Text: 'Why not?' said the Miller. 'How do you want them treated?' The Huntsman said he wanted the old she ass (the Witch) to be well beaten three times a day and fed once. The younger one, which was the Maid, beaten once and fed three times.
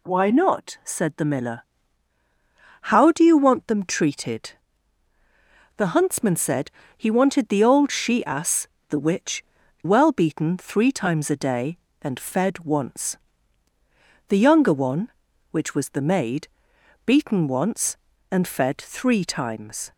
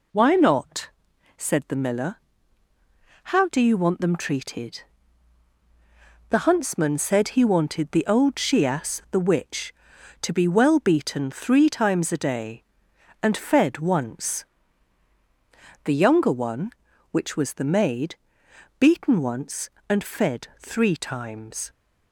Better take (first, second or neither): second